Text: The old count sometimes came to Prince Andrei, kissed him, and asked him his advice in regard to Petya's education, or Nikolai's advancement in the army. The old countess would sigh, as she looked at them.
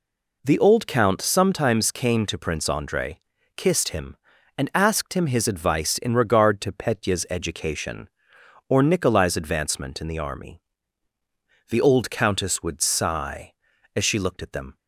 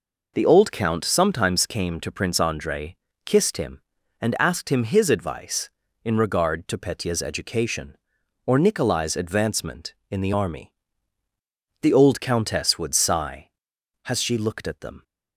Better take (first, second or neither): first